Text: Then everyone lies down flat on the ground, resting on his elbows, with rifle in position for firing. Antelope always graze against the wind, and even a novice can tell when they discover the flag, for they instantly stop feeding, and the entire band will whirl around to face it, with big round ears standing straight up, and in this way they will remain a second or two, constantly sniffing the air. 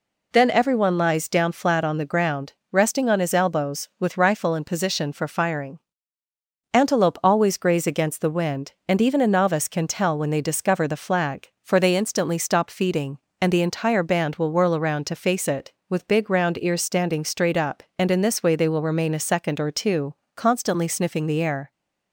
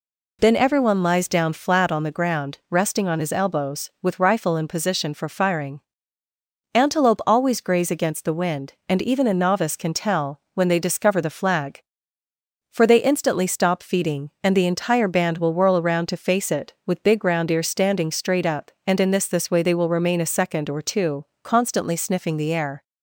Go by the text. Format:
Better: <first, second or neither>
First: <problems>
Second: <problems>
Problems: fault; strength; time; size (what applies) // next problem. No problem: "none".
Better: first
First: none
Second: pauses between "tell" and "when"; slight; at 10.3 s; 0.16 s long // says "this" twice; at 19.2 s